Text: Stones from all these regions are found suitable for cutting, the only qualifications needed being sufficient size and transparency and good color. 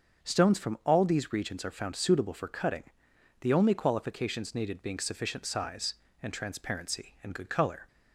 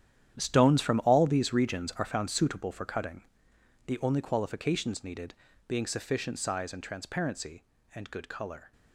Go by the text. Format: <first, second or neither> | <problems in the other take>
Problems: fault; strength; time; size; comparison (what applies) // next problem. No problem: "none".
first | gets quieter; strong; throughout; 13.5 dB // starts louder than the rest; strong; until 1.4 s; 10.5 dB; also in the first // pauses between "needed" and "being"; slight; at 5.3 s; 0.34 s long